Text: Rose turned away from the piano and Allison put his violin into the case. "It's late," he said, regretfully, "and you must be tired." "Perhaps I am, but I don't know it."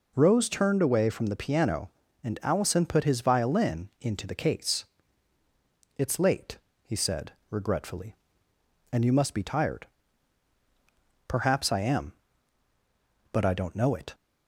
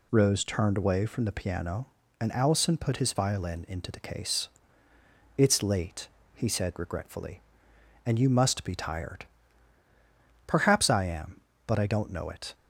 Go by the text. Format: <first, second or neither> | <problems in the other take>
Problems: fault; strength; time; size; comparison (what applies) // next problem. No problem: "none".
neither | none